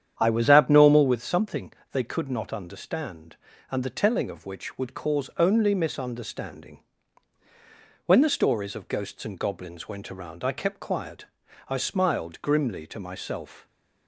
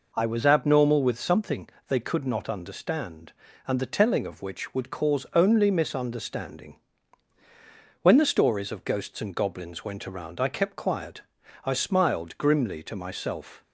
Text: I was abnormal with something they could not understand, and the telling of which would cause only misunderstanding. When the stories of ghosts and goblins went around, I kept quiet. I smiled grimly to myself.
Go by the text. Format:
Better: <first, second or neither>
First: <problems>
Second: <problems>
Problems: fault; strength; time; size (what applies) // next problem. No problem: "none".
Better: second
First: starts louder than the rest; strong; until 1.1 s; 9 dB // pauses between "something" and "they"; slight; at 1.7 s; 0.18 s long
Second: pauses between "something" and "they"; slight; at 1.7 s; 0.18 s long